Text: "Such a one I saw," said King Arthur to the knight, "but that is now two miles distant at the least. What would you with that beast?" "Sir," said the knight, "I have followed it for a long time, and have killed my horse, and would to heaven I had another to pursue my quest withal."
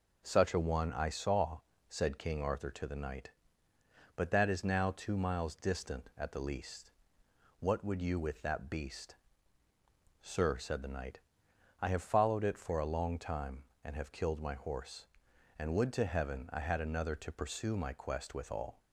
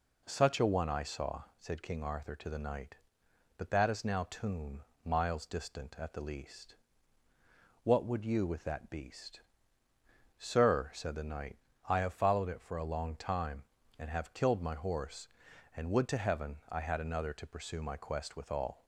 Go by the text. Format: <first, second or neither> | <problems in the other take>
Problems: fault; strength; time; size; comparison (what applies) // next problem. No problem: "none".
first | says "tomb" for "two"; at 4.2 s